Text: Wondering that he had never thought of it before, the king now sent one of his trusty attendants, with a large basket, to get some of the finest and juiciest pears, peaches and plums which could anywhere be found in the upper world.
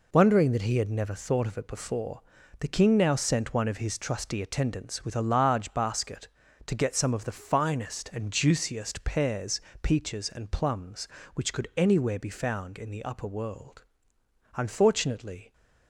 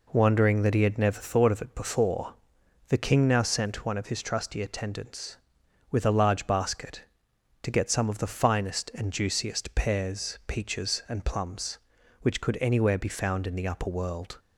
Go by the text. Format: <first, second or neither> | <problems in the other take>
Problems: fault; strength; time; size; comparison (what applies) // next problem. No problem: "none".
second | goes on to say "Unfortunately"; noticeable; from 14.5 s on; 0.98 s long